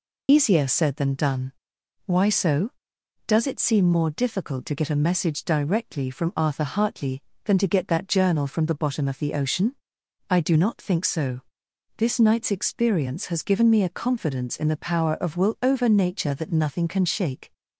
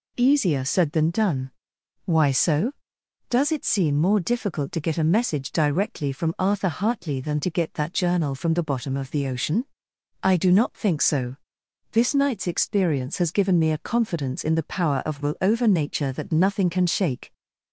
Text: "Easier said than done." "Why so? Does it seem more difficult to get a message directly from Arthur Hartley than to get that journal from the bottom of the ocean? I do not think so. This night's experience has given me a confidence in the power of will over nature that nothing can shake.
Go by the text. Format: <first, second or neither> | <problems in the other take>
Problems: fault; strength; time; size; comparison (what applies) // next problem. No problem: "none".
second | loses the start of "Easier"; at 0.2 s; 70 ms